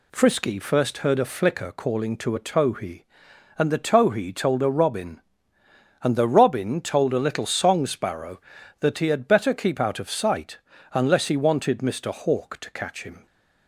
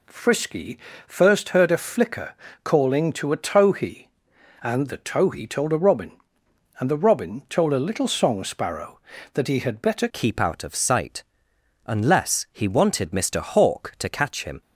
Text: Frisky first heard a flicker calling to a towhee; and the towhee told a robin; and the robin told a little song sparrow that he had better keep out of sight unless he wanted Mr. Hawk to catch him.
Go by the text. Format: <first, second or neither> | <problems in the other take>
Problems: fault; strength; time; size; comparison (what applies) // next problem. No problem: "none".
first | pauses between "Frisky" and "first"; slight; at 0.7 s; 0.30 s long // pauses between "flicker" and "calling"; slight; at 2.3 s; 0.30 s long // changes voice at "keep"; from 10.1 s on; 4.5 s long // pauses between "sight" and "unless"; noticeable; at 11.2 s; 0.60 s long; slight in the first